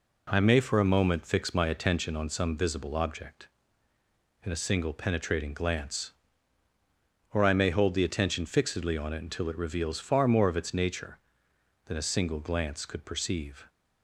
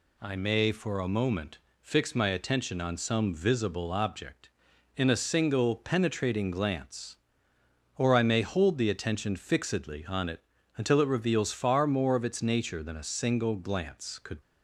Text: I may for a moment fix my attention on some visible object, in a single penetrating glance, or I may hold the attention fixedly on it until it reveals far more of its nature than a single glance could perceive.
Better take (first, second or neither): first